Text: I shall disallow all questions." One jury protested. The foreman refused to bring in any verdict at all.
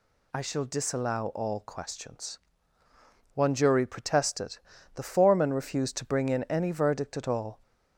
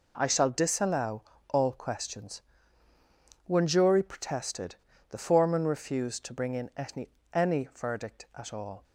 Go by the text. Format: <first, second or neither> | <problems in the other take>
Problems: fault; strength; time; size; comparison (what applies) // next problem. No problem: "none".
first | pauses between "disallow" and "all"; slight; at 1.2 s; 0.26 s long // says "any" twice; at 7.3 s